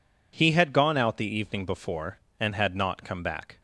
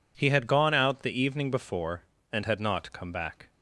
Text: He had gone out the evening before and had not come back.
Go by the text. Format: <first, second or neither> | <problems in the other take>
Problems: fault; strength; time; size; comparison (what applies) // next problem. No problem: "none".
neither | none